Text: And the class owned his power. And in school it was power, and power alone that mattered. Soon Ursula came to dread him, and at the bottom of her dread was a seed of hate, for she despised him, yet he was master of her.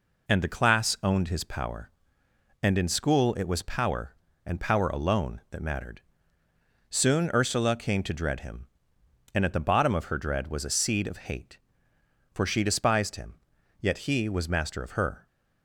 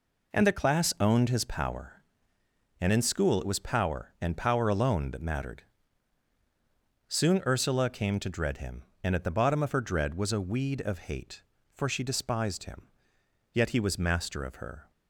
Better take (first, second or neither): first